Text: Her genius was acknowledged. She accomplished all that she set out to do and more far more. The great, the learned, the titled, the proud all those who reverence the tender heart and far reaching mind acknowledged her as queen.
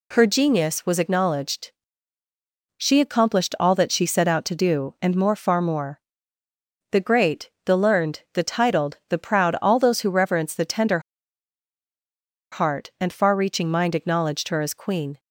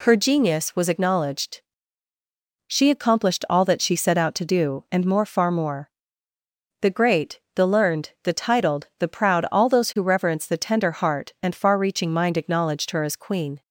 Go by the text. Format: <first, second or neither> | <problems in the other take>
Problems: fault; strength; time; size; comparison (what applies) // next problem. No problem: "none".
second | pauses between "tender" and "heart"; strong; at 10.9 s; 1.5 s long